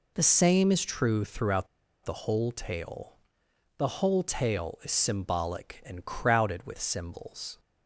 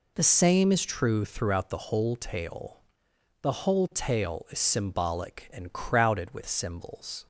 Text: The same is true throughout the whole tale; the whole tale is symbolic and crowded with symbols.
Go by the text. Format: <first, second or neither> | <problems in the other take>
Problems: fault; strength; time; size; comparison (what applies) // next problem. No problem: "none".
second | pauses between "throughout" and "the"; at 1.6 s; 0.38 s long